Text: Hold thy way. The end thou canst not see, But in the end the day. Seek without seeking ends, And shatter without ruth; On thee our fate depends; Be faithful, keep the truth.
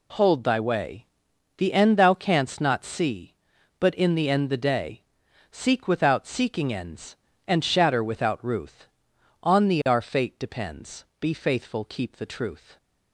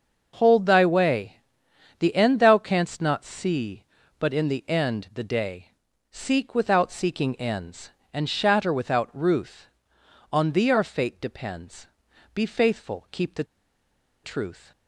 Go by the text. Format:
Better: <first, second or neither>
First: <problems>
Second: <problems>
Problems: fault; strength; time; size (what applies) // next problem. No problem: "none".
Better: first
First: none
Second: starts louder than the rest; noticeable; until 1.3 s; 6 dB // pauses between "the" and "truth"; noticeable; at 13.4 s; 0.79 s long